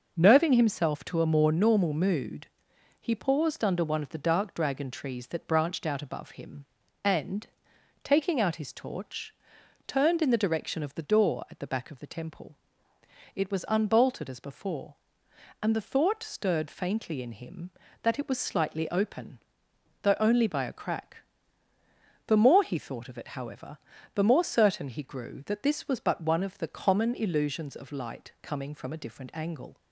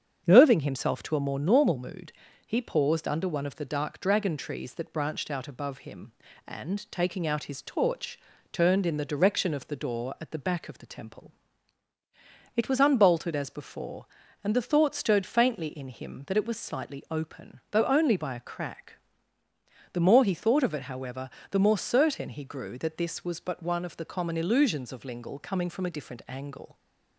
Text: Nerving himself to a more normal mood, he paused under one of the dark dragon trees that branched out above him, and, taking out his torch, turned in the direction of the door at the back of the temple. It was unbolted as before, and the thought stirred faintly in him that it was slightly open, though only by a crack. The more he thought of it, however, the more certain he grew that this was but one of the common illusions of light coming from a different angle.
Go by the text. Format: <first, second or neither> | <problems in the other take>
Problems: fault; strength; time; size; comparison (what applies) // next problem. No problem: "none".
first | starts louder than the rest; strong; until 1.2 s; 7.5 dB // says "lingle" for "light"; at 25.0 s